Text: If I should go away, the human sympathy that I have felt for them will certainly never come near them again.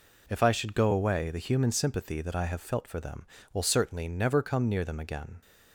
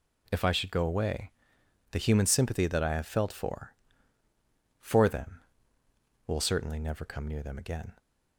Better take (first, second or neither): first